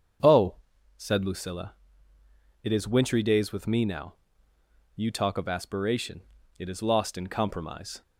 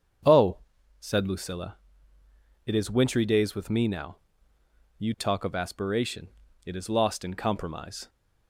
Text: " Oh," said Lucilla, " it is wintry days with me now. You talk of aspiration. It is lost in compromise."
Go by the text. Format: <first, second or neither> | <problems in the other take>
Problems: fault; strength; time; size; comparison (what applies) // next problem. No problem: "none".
neither | starts louder than the rest; strong; the same in both